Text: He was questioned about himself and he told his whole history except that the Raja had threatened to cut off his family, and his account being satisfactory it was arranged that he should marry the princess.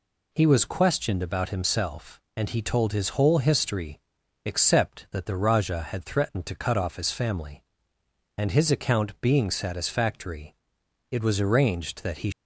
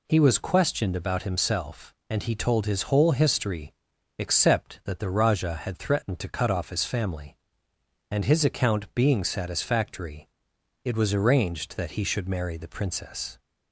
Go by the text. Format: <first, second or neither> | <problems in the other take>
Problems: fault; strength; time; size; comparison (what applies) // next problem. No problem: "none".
second | pauses between "history" and "except"; noticeable; at 3.9 s; 0.46 s long; noticeable in the second // pauses between "satisfactory" and "it"; noticeable; at 10.5 s; 0.56 s long; noticeable in the second // stops before "should marry the princess"; at 12.3 s